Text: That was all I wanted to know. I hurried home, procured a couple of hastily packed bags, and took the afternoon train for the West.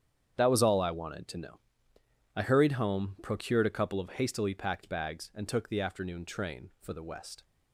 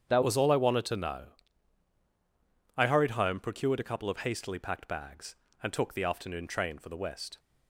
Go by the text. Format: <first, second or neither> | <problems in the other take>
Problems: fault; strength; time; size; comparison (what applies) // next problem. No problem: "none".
first | starts louder than the rest; strong; until 1.0 s; 8 dB; strong in the first // changes voice at "was"; from 0.2 s on; 7.1 s long